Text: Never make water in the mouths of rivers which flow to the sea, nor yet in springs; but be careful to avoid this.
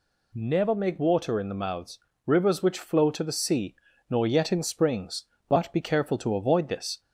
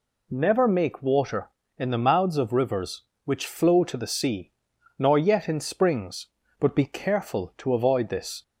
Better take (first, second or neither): second